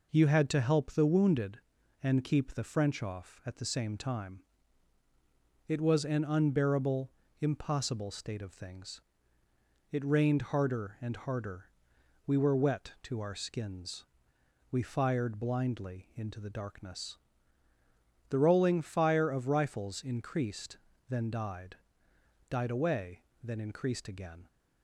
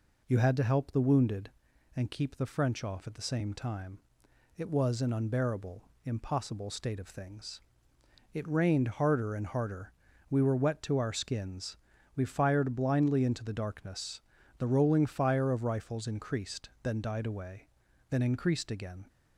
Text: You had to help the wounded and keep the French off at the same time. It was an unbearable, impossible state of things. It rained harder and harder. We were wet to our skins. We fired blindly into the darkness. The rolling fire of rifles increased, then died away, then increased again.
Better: second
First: says "died" twice; at 22.4 s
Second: none

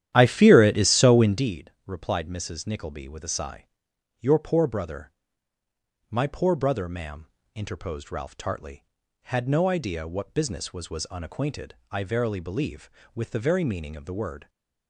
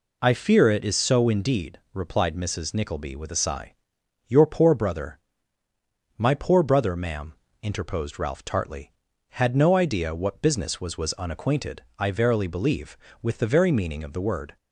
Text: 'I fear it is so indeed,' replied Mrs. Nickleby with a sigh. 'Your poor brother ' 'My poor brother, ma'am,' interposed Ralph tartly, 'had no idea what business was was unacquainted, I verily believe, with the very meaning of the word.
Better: second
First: starts louder than the rest; strong; until 1.5 s; 11.5 dB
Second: none

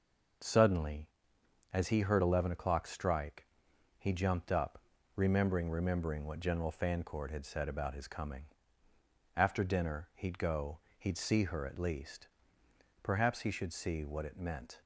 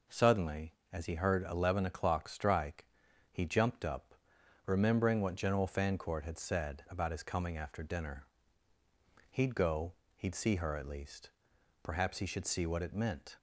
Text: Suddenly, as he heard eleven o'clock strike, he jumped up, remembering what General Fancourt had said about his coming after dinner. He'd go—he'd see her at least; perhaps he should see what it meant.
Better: second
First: says "remembering" twice; at 5.7 s // pauses between "coming" and "after"; noticeable; at 8.4 s; 0.90 s long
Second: none

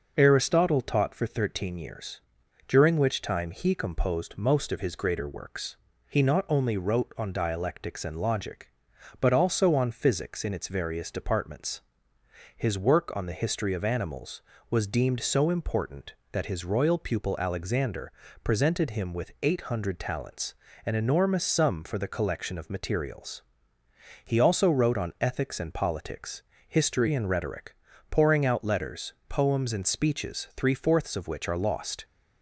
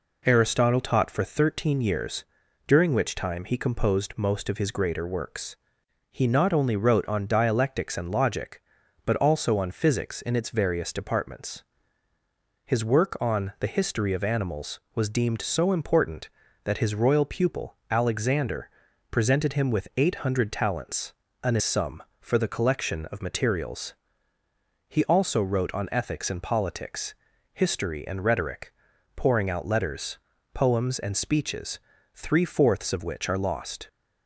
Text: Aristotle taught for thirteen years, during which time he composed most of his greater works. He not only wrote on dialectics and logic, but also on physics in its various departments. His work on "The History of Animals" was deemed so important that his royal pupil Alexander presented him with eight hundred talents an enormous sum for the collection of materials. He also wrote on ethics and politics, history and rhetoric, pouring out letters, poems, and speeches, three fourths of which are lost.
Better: first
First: pauses between "Alexander" and "presented"; slight; at 18.1 s; 0.32 s long // pauses between "talents" and "an"; slight; at 20.5 s; 0.30 s long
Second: pauses between "Alexander" and "presented"; at 18.6 s; 0.42 s long // pauses between "talents" and "an"; slight; at 21.1 s; 0.30 s long // skips "enormous"; at 21.5 s

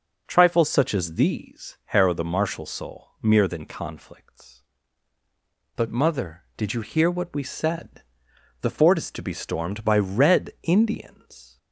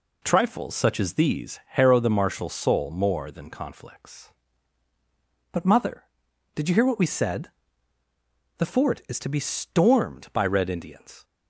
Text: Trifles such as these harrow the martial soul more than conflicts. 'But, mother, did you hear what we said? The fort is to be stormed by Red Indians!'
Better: second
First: says "mere" for "more"; at 3.2 s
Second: none

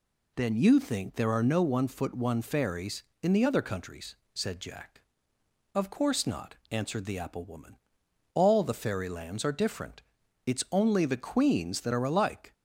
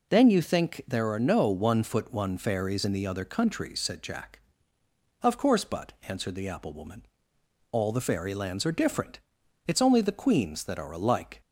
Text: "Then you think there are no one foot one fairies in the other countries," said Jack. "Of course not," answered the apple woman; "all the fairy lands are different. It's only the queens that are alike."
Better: first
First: none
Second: says "but" for "not"; at 5.6 s

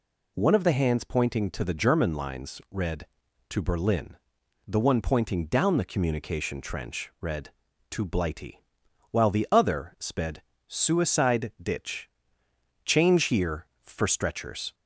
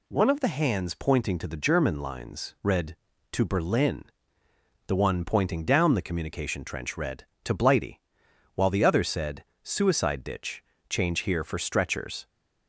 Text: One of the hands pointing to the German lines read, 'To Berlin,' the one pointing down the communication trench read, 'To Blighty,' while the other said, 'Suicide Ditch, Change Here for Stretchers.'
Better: second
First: says "sped" for "said"; at 9.9 s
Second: none

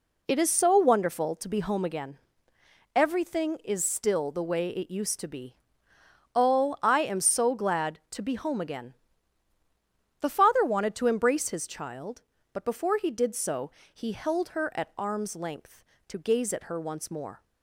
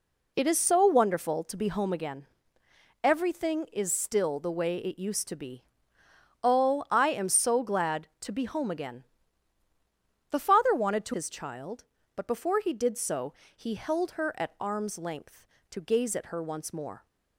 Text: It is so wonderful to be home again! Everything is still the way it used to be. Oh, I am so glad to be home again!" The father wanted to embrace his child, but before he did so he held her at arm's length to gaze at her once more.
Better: first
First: pauses between "so" and "he"; slight; at 13.6 s; 0.24 s long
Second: skips "embrace"; at 11.1 s // pauses between "so" and "he"; slight; at 13.3 s; 0.24 s long

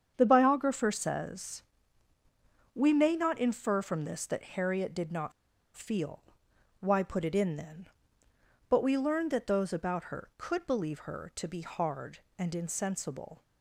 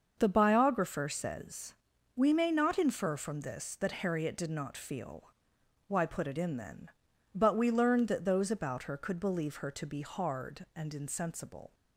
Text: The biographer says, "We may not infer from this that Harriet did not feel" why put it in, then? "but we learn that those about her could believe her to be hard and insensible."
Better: second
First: starts louder than the rest; strong; until 1.1 s; 7.5 dB // pauses between "not" and "feel"; at 5.3 s; 0.44 s long // pauses between "feel" and "why"; noticeable; at 6.2 s; 0.58 s long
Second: starts louder than the rest; until 1.2 s; 6.5 dB // pauses between "feel" and "why"; noticeable; at 5.2 s; 0.56 s long

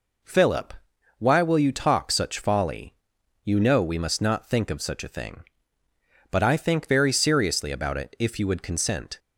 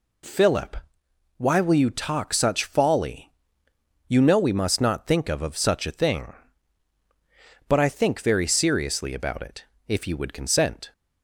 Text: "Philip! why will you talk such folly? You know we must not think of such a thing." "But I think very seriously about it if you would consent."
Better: first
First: none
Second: says "of" twice; at 5.4 s // pauses between "it" and "if"; slight; at 9.6 s; 0.20 s long

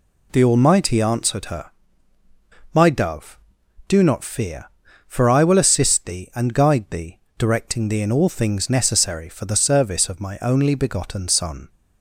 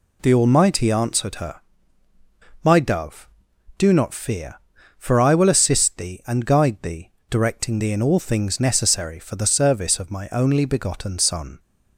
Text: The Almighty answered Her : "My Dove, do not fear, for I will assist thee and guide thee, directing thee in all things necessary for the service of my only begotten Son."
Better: neither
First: none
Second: none

